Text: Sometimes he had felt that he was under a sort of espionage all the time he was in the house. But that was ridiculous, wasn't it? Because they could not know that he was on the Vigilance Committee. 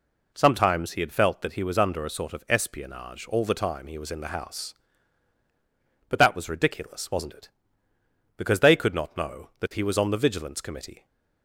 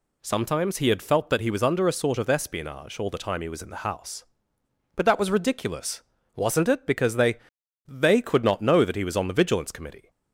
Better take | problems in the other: first | says "they" twice; at 7.8 s

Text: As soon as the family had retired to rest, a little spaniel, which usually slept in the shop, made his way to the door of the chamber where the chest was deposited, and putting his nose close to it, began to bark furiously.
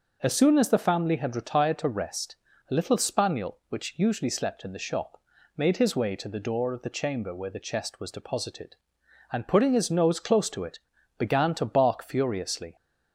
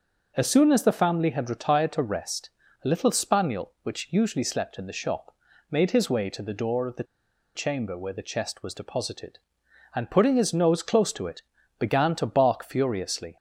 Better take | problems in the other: first | pauses between "the" and "chamber"; noticeable; at 7.0 s; 0.52 s long

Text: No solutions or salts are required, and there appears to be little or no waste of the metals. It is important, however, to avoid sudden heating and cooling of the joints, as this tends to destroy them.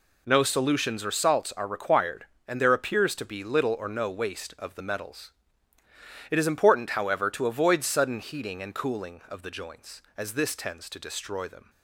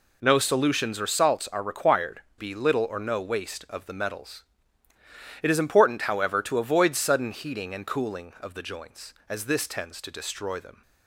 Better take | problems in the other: first | skips "and there appears to"; at 2.3 s

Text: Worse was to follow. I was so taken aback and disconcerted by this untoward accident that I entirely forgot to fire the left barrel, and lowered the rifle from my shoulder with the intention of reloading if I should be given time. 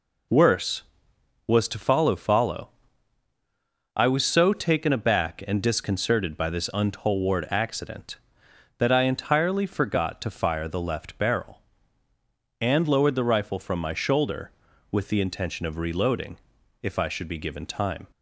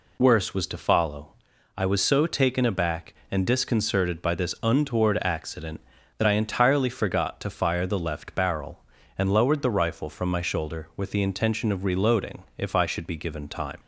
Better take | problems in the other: second | says "follow" twice; at 2.1 s // pauses between "reloading" and "if"; at 16.3 s; 0.44 s long; slight in the second

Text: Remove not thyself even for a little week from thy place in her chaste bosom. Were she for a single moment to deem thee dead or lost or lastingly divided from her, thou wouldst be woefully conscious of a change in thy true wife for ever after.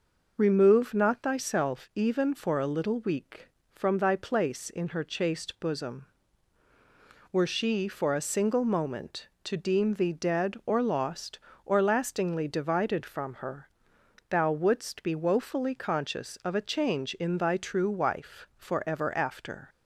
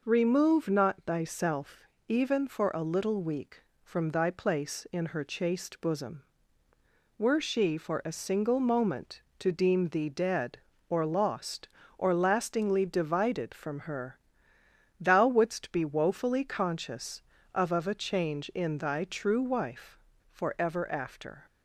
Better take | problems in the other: first | pauses between "thyself" and "even"; slight; at 1.8 s; 0.24 s long // says "of" twice; at 17.7 s

